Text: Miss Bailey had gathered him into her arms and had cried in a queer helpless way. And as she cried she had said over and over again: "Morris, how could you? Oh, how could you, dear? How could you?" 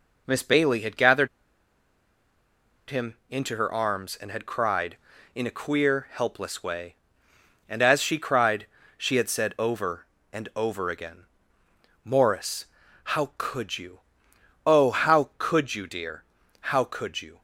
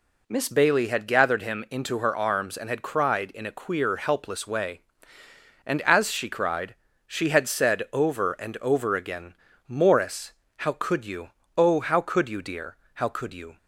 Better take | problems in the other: second | pauses between "gathered" and "him"; strong; at 1.2 s; 1.6 s long // pauses between "him" and "into"; slight; at 3.1 s; 0.16 s long // pauses between "cried" and "she"; slight; at 8.6 s; 0.30 s long; slight in the second

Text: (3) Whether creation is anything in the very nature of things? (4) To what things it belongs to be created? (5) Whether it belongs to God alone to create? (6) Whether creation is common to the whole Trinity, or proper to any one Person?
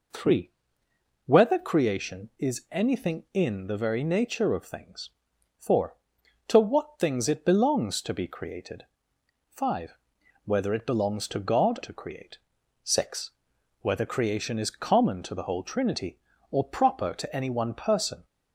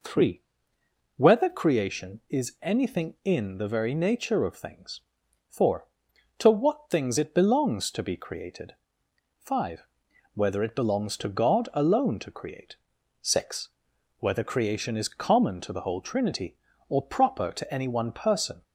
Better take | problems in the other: second | skips "alone"; at 11.8 s

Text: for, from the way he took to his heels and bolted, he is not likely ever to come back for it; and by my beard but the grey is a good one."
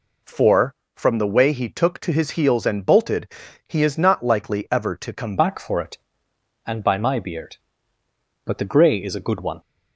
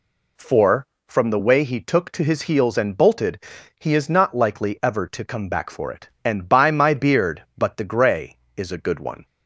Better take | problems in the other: second | changes voice at "back"; from 5.3 s on; 4.2 s long

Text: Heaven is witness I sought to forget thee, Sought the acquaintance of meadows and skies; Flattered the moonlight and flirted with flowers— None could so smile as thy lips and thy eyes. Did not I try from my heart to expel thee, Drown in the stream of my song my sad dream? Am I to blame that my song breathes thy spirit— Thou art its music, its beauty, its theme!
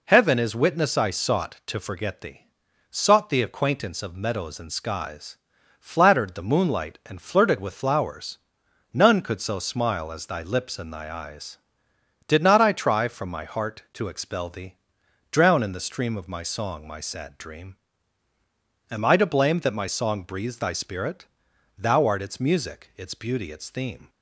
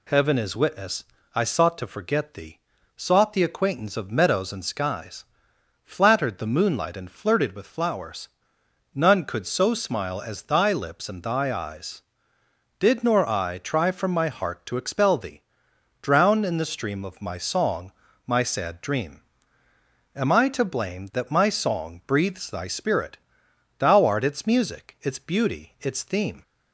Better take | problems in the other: first | pauses between "witness" and "I"; slight; at 1.0 s; 0.32 s long // says "nor" for "not"; at 13.0 s // pauses between "song" and "my"; slight; at 17.9 s; 0.34 s long

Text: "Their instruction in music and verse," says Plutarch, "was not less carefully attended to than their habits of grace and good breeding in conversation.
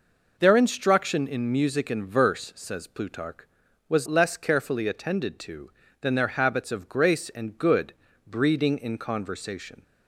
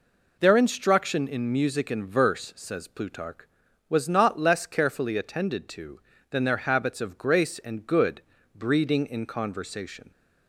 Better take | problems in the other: second | skips "not"; at 4.0 s // pauses between "good" and "breeding"; slight; at 7.9 s; 0.32 s long; slight in the second

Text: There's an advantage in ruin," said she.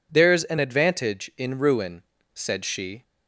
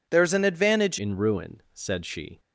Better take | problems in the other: first | changes voice at "in"; from 0.9 s on; 1.4 s long

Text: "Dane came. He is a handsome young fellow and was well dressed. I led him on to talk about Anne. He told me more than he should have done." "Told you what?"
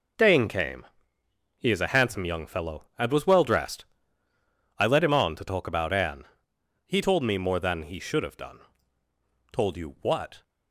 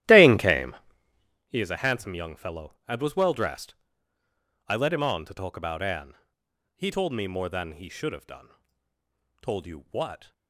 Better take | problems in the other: first | starts louder than the rest; strong; until 1.4 s; 13.5 dB

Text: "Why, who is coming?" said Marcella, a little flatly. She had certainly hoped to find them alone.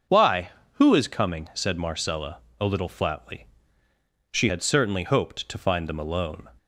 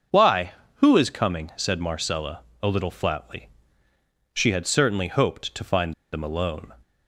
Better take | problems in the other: first | starts louder than the rest; until 1.3 s; 6 dB // pauses between "find" and "them"; slight; at 5.9 s; 0.20 s long

